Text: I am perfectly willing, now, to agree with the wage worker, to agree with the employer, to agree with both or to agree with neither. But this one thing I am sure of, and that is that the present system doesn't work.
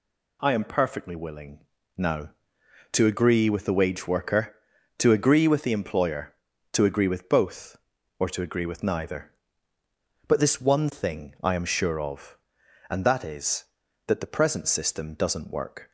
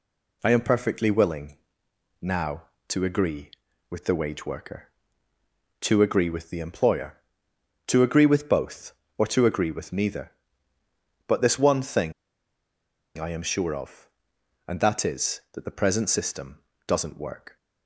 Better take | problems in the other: first | pauses between "thing" and "I"; at 12.1 s; 1.0 s long // pauses between "system" and "doesn't"; slight; at 16.5 s; 0.28 s long

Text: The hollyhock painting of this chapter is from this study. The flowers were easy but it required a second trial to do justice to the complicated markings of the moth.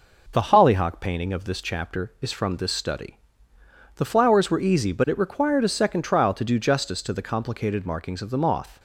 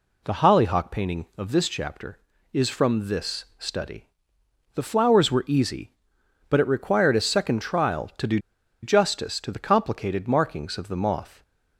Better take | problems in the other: first | pauses between "do" and "justice"; at 8.3 s; 0.44 s long

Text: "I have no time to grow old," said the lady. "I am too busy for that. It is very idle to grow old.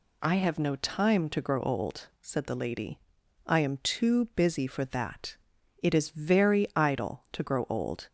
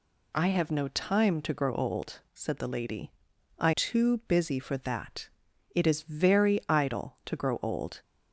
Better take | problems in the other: first | skips "am"; at 3.7 s

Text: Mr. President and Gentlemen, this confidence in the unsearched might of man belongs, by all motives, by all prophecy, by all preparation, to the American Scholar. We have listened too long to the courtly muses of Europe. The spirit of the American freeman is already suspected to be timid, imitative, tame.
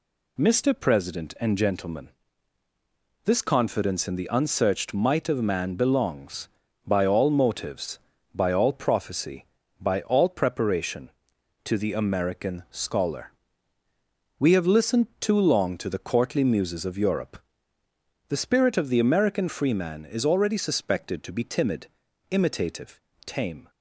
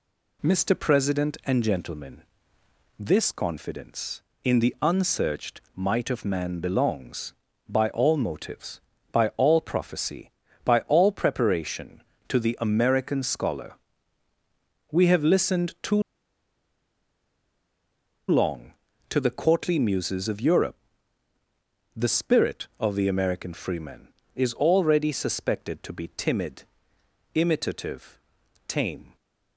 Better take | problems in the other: first | pauses between "unsearched" and "might"; slight; at 5.5 s; 0.16 s long // pauses between "too" and "long"; strong; at 16.0 s; 2.2 s long

